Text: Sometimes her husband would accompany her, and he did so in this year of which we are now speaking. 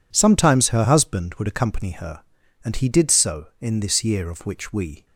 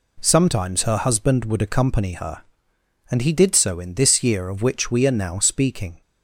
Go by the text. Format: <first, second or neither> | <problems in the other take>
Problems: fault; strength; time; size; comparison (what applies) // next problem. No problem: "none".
second | stops before "are now speaking"; at 5.0 s